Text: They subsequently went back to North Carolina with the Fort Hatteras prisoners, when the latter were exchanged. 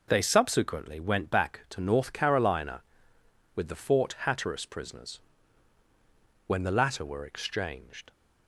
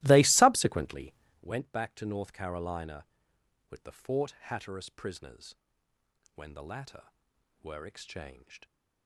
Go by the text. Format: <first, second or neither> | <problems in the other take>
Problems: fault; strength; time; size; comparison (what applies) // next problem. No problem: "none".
first | starts louder than the rest; strong; until 1.5 s; 18 dB // pauses between "subsequently" and "went"; slight; at 1.1 s; 0.30 s long